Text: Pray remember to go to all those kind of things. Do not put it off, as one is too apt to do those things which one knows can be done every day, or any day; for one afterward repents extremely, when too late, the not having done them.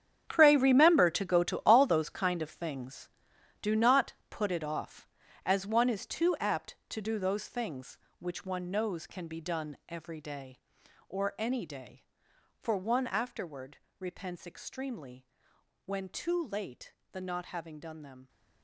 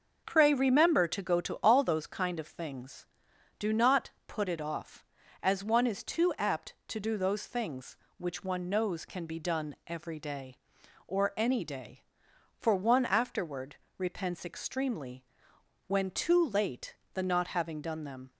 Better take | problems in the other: second | gets quieter; strong; throughout; 13.5 dB // starts louder than the rest; strong; until 1.2 s; 8.5 dB; also in the second // pauses between "not" and "put"; slight; at 4.1 s; 0.16 s long; slight in the second // pauses between "afterward" and "repents"; slight; at 13.7 s; 0.22 s long; slight in the second

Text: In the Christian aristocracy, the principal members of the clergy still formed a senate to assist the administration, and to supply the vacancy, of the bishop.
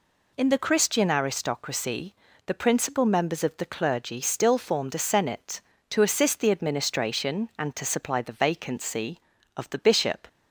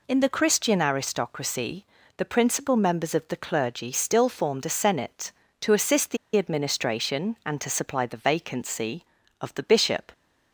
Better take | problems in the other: first | pauses between "the" and "administration"; slight; at 6.1 s; 0.19 s long

